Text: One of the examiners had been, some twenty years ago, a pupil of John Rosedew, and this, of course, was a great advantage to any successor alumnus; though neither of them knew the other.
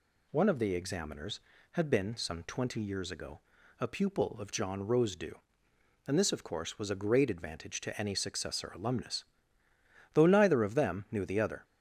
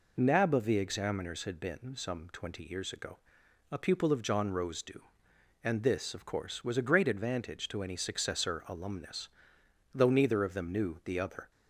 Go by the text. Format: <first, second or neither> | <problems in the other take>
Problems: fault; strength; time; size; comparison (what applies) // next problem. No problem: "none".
first | says "Nab" for "One"; at 0.1 s